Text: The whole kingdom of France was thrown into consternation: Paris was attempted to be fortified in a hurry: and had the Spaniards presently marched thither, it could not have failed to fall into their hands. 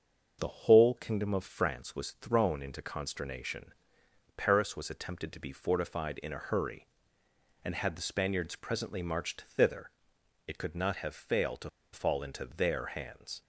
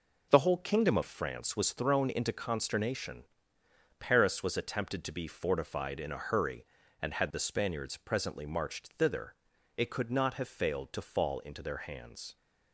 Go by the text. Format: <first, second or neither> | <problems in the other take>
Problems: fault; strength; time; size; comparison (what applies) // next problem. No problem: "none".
second | starts louder than the rest; until 1.4 s; 6.5 dB // pauses between "to" and "fall"; slight; at 11.6 s; 0.23 s long